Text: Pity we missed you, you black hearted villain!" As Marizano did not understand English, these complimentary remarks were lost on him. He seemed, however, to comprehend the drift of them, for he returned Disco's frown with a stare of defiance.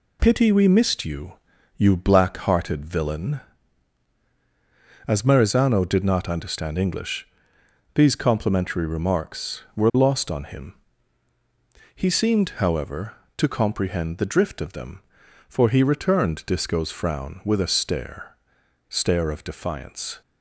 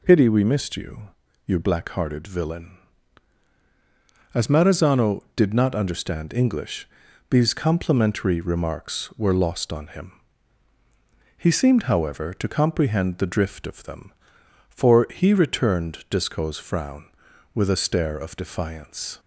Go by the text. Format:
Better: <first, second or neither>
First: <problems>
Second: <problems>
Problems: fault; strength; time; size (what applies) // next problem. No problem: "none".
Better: second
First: says "stare" twice; at 18.8 s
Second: none